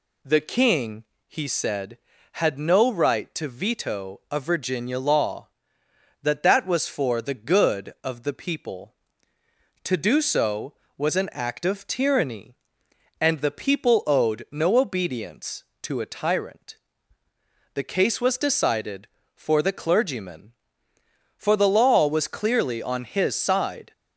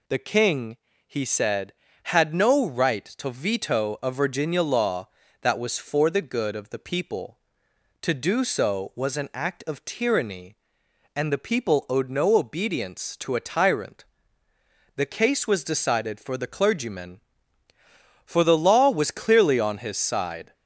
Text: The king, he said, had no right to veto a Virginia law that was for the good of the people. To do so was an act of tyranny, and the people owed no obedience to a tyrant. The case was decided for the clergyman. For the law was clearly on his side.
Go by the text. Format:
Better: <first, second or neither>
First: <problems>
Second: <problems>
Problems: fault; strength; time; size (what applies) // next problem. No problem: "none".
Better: second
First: says "that" twice; at 6.4 s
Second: none